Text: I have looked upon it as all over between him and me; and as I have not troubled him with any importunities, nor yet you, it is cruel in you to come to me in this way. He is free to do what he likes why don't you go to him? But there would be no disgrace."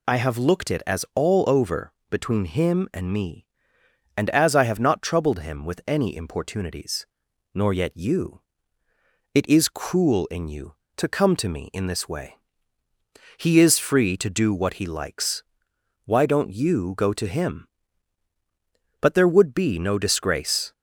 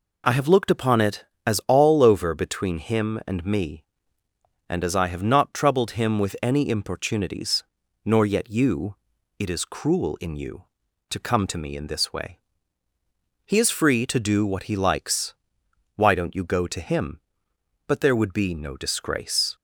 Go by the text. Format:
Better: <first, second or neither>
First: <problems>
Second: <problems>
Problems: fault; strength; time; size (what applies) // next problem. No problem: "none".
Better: second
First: skips "upon"; at 0.7 s // pauses between "over" and "between"; slight; at 1.9 s; 0.18 s long // pauses between "likes" and "why"; noticeable; at 15.4 s; 0.60 s long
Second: pauses between "likes" and "why"; noticeable; at 15.3 s; 0.60 s long